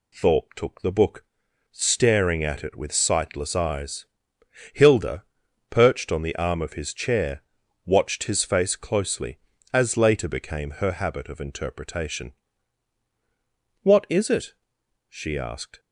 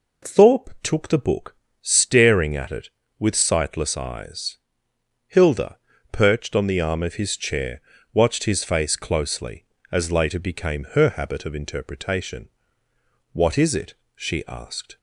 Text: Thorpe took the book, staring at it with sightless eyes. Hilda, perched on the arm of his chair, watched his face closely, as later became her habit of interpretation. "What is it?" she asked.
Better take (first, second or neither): neither